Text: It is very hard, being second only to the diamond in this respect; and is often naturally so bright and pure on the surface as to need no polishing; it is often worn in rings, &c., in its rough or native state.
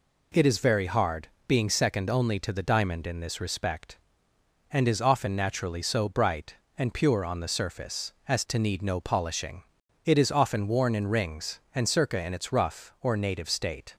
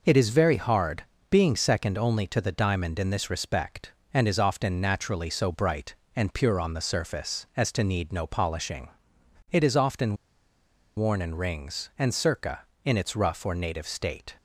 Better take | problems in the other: first | pauses between "often" and "worn"; noticeable; at 10.1 s; 0.80 s long

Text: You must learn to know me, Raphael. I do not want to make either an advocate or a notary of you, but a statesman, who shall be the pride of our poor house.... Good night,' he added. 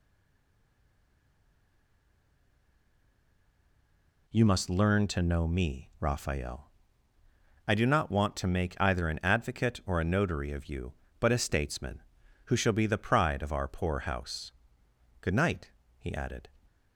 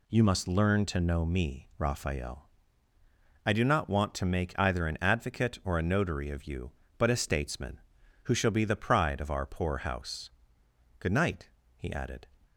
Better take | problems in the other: second | stays silent before the first word; strong; until 4.2 s; 4.2 s long

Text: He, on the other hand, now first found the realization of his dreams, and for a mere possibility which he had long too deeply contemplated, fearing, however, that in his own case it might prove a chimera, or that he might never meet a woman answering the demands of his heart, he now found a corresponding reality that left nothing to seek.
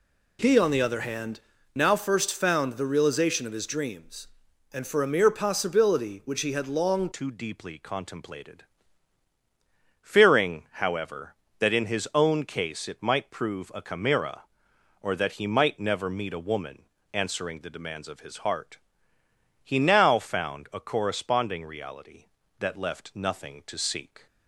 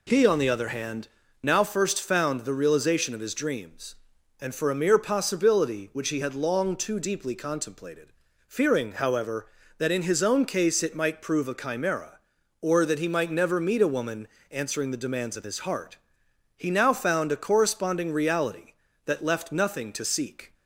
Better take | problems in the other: second | changes voice at "too"; from 7.1 s on; 17.1 s long // pauses between "woman" and "answering"; slight; at 16.8 s; 0.30 s long; slight in the second

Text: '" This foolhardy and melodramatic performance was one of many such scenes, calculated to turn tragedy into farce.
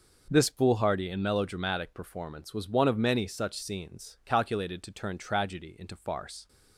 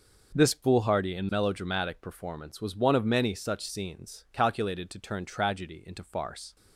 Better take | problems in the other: neither | none

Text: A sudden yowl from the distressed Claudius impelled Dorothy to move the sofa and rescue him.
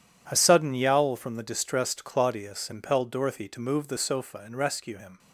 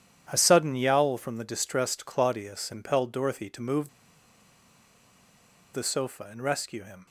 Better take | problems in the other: first | pauses between "move" and "the"; strong; at 3.8 s; 1.8 s long

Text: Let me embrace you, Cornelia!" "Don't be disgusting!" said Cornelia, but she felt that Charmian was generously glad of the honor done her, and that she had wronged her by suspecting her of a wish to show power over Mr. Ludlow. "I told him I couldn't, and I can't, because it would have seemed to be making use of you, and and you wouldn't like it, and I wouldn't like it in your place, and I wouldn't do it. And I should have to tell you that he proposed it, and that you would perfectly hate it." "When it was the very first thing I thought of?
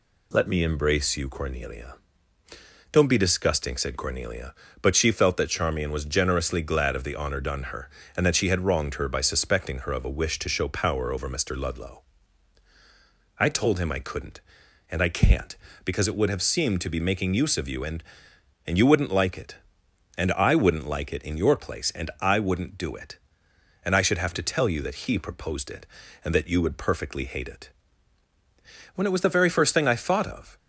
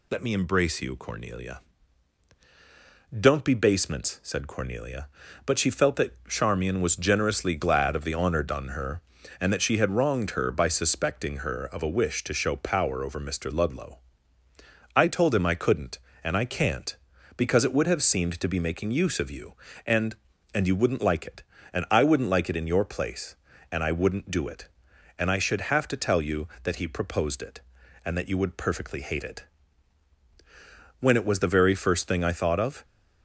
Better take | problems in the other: first | says "basements" for "disgusting"; at 3.5 s

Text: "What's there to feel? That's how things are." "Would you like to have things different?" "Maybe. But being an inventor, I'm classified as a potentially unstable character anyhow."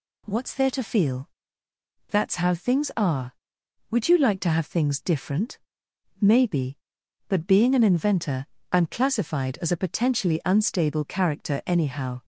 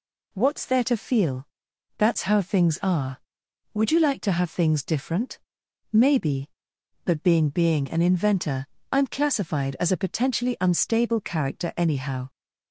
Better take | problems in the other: first | says "being" twice; at 7.4 s

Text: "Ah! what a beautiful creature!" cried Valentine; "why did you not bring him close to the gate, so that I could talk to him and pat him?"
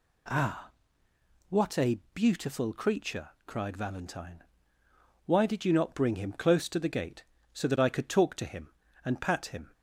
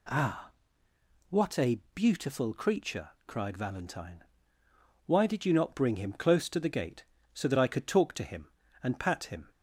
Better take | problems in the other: neither | none

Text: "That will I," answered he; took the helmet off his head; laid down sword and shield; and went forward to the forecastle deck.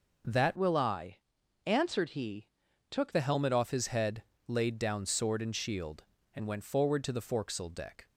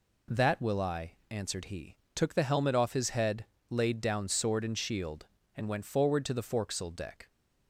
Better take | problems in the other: second | changes voice from "will" to "took"; from 0.5 to 3.1 s; 2.6 s long

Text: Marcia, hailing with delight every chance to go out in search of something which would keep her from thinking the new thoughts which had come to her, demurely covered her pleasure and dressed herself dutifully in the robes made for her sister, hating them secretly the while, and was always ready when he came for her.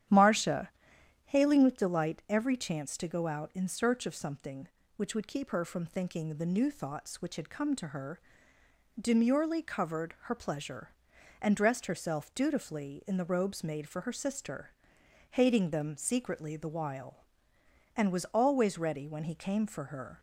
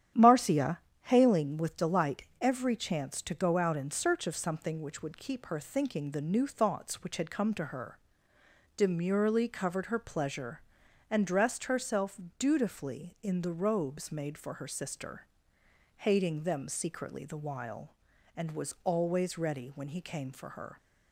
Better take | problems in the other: first | starts louder than the rest; strong; until 1.4 s; 10 dB; strong in the first // pauses between "delight" and "every"; slight; at 2.2 s; 0.18 s long // skips "from"; at 5.5 s // pauses between "herself" and "dutifully"; slight; at 12.1 s; 0.18 s long

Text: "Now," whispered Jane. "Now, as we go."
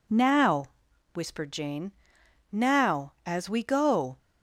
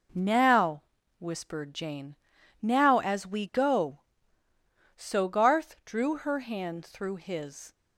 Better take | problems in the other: first | goes on to say "So Garth drew her hand through his"; strong; from 4.9 s on; 2.7 s long

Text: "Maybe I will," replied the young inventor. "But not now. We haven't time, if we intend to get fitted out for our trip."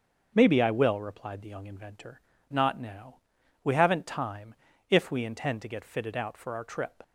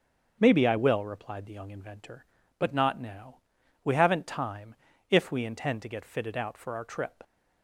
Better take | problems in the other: second | starts louder than the rest; until 1.3 s; 6.5 dB; also in the second // skips "But"; at 2.3 s

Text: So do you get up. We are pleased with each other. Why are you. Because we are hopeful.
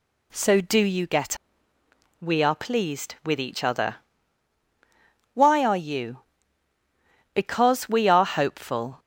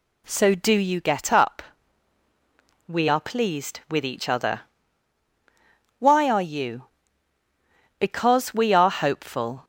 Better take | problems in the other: second | skips "up"; at 1.7 s

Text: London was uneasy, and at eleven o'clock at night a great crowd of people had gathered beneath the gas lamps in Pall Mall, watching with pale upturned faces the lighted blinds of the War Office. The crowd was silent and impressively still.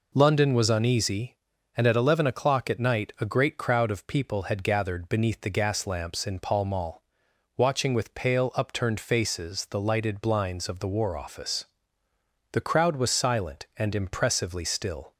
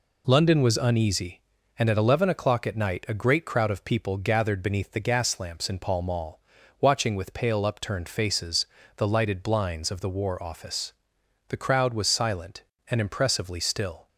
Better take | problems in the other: first | skips "had"; at 4.1 s // pauses between "faces" and "the"; slight; at 8.6 s; 0.30 s long

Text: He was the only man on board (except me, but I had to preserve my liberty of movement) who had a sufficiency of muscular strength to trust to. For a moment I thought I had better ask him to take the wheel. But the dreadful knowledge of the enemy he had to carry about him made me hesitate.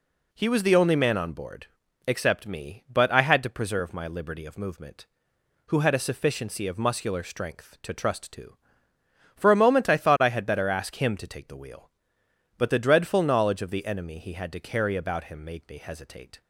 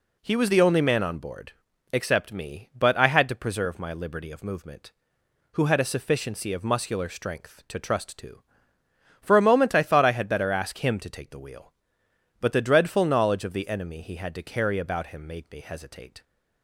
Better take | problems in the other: neither | none

